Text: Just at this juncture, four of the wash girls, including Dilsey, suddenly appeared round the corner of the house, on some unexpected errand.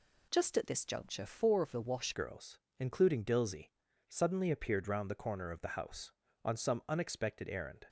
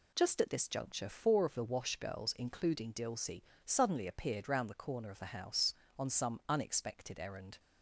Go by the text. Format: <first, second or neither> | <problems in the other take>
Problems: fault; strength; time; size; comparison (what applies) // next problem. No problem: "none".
second | changes voice at "girls"; from 2.1 s on; 5.7 s long